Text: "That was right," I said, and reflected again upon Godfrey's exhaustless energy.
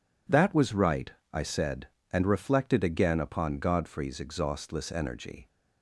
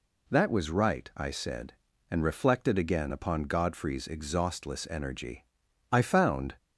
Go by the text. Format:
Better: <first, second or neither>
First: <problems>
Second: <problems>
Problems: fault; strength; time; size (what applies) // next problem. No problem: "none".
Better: first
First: none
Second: goes on to say "I found"; noticeable; from 5.9 s on; 0.62 s long